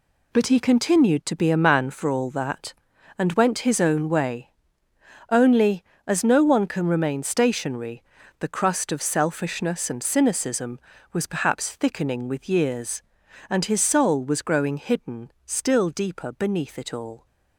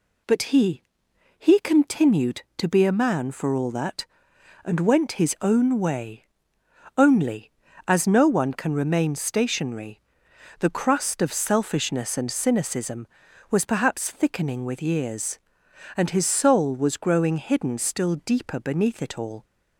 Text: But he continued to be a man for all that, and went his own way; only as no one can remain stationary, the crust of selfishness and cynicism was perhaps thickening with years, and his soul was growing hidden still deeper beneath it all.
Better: first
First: none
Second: says "he" twice; at 1.3 s

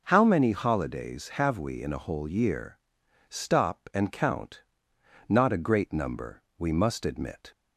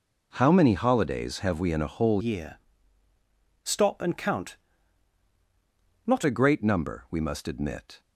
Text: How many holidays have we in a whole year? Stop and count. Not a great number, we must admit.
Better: first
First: none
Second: changes voice from "year" to "Not"; from 2.2 to 6.2 s; 4.0 s long

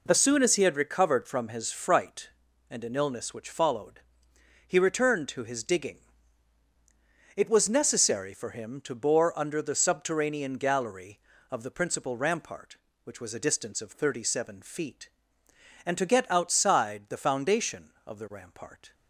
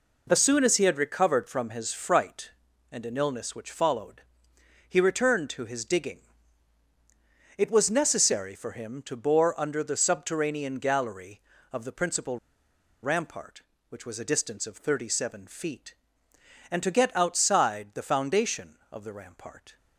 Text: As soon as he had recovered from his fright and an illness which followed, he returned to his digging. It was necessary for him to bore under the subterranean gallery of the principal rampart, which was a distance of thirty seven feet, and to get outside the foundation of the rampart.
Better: first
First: none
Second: pauses between "principal" and "rampart"; noticeable; at 12.3 s; 0.66 s long

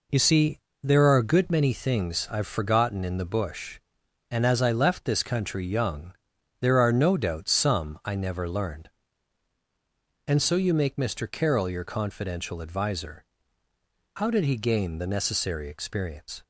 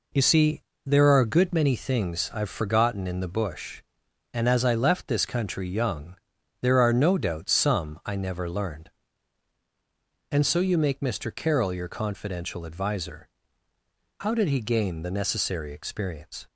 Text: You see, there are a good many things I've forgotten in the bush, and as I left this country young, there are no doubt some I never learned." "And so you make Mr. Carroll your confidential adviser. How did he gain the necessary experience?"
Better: neither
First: none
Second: none

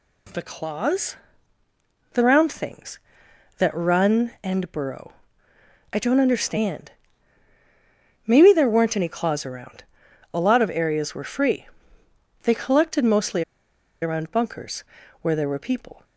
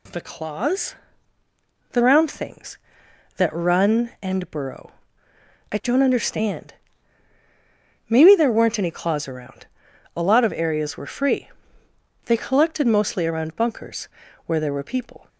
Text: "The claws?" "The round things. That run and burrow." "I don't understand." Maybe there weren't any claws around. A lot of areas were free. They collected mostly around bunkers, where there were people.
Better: second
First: pauses between "mostly" and "around"; noticeable; at 13.4 s; 0.60 s long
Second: none

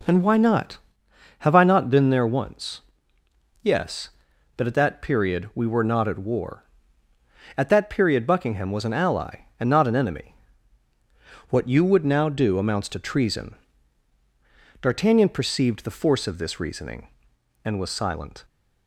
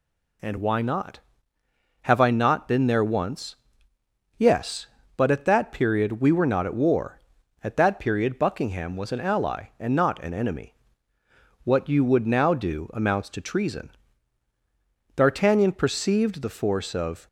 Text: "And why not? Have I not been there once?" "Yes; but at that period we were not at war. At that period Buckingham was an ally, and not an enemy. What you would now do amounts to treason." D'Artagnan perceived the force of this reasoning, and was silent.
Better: first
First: none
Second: stops before "this reasoning and was silent"; at 17.2 s

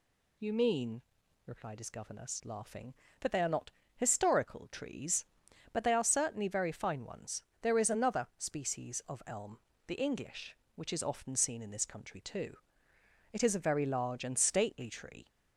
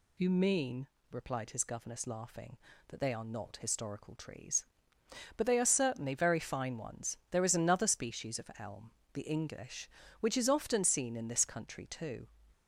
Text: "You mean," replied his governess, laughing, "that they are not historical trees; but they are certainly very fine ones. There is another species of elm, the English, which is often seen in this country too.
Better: second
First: pauses between "not" and "historical"; slight; at 3.7 s; 0.24 s long // goes on to say "It is a very large and stately tree"; strong; from 13.3 s on; 1.9 s long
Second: none

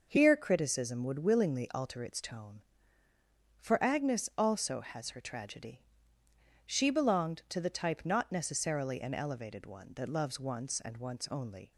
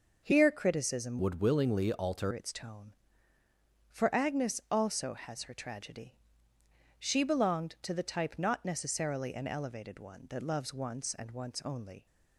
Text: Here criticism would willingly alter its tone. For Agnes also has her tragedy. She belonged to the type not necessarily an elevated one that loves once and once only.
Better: first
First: none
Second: changes voice from "would" to "alter"; from 1.1 to 2.3 s; 1.2 s long

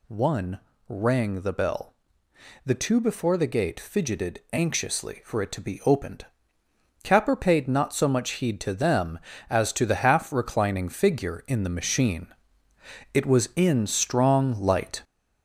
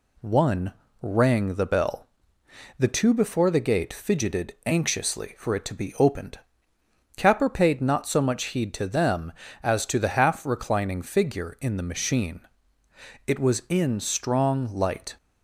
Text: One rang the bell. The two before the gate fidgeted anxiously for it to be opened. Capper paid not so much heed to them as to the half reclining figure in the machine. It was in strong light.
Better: second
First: gets louder; throughout; 6.5 dB // pauses between "One" and "rang"; slight; at 0.6 s; 0.26 s long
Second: pauses between "One" and "rang"; slight; at 0.7 s; 0.26 s long

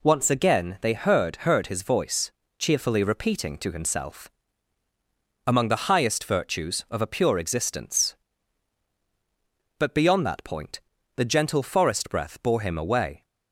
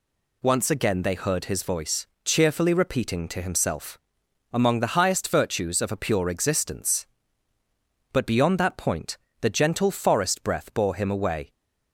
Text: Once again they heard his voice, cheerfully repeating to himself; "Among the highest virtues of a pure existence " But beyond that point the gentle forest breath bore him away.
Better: second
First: says "heard" twice; at 1.3 s // pauses between "point" and "the"; at 10.7 s; 0.38 s long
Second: pauses between "point" and "the"; slight; at 9.1 s; 0.24 s long

